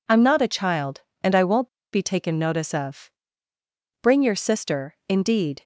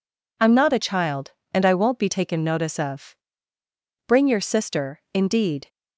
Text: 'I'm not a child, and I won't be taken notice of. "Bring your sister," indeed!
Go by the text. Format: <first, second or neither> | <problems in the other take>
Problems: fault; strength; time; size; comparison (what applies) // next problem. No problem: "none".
second | pauses between "won't" and "be"; slight; at 1.6 s; 0.24 s long